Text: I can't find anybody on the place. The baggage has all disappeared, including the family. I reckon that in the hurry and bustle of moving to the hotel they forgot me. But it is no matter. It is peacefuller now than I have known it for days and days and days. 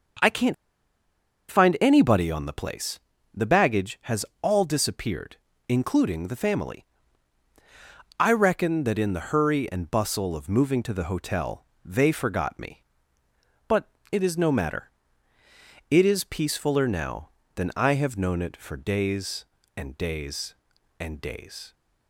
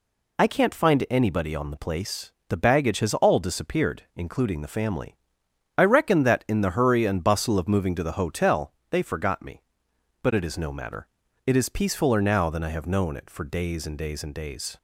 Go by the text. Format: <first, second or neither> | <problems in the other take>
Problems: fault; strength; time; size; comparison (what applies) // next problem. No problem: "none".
second | starts louder than the rest; until 2.2 s; 6.5 dB // pauses between "can't" and "find"; noticeable; at 0.5 s; 0.96 s long // pauses between "has" and "all"; slight; at 4.2 s; 0.16 s long // pauses between "hotel" and "they"; slight; at 11.6 s; 0.18 s long; slight in the second // pauses between "But" and "it"; slight; at 13.8 s; 0.24 s long